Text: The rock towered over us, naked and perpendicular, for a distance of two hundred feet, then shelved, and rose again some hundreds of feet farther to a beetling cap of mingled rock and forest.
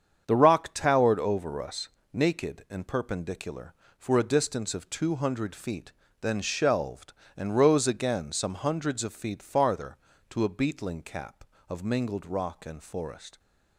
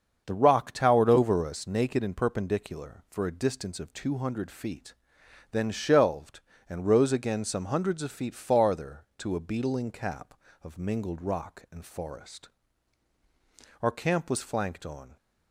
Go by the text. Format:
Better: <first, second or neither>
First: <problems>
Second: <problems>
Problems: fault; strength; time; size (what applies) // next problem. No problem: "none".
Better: first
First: starts louder than the rest; strong; until 1.2 s; 7.5 dB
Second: starts louder than the rest; until 1.2 s; 7 dB // goes on to say "Our camp was flanked on"; from 13.8 s on; 1.3 s long